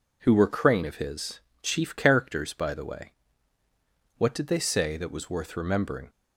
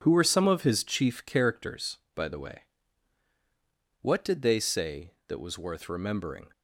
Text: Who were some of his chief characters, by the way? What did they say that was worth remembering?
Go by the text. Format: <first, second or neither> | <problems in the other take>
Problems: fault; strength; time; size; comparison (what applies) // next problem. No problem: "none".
second | says "crane" for "some"; at 0.4 s // pauses between "his" and "chief"; slight; at 1.4 s; 0.20 s long